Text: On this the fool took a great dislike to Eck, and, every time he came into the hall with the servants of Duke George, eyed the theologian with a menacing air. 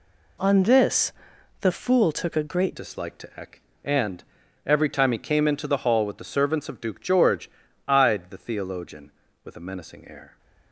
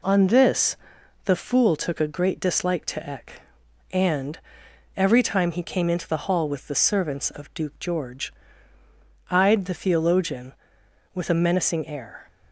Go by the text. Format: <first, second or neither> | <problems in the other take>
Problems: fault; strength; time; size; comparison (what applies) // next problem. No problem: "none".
second | pauses between "this" and "the"; noticeable; at 1.1 s; 0.50 s long; noticeable in the second // changes voice at "dislike"; from 2.7 s on; 7.6 s long